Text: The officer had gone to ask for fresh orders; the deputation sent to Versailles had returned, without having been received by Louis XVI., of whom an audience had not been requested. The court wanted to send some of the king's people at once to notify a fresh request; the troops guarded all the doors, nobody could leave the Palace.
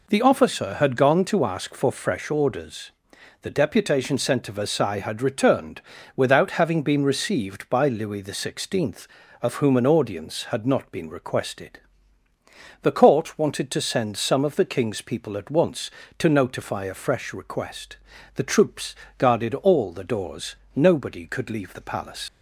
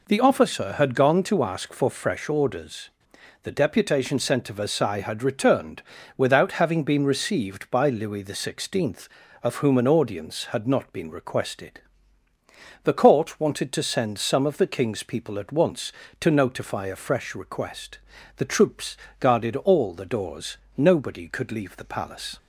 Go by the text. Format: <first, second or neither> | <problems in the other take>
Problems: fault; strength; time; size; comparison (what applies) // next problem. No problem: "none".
second | pauses between "troops" and "guarded"; slight; at 18.9 s; 0.22 s long; slight in the second // leaves "Palace" unfinished; at 22.2 s; 60 ms